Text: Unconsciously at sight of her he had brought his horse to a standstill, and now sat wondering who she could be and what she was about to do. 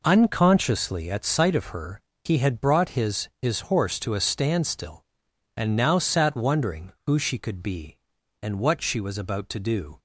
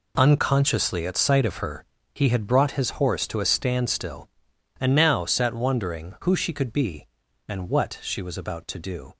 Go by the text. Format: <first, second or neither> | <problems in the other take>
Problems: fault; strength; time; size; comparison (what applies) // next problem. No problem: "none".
second | pauses between "her" and "he"; slight; at 2.0 s; 0.24 s long; slight in the second // says "his" twice; at 3.4 s